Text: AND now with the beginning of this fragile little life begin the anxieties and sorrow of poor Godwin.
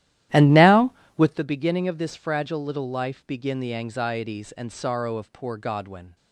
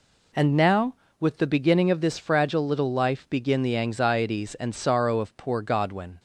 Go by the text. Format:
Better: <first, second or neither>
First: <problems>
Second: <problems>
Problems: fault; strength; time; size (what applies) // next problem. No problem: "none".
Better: second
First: starts louder than the rest; strong; until 1.4 s; 13 dB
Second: none